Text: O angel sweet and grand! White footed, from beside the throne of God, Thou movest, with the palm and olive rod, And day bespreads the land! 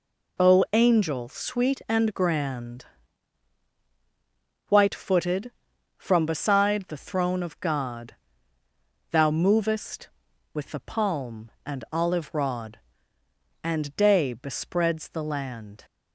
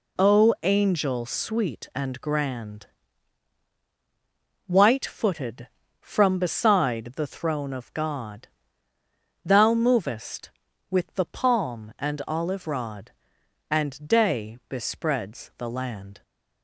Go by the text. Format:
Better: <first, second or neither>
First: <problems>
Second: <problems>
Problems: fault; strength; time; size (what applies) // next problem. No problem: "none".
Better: neither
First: none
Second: none